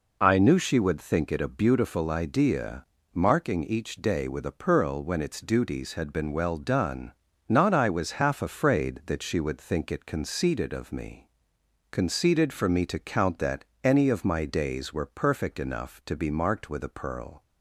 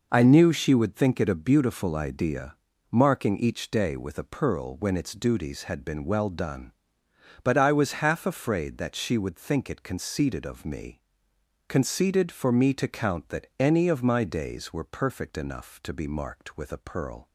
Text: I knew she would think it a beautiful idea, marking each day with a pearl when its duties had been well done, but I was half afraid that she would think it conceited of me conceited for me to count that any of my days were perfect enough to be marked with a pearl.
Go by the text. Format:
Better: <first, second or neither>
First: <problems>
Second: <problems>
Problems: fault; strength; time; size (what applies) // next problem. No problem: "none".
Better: second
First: says "not" for "but"; at 7.4 s // pauses between "me" and "conceited"; noticeable; at 11.2 s; 0.64 s long // pauses between "that" and "any"; slight; at 13.6 s; 0.18 s long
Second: pauses between "me" and "conceited"; noticeable; at 11.0 s; 0.66 s long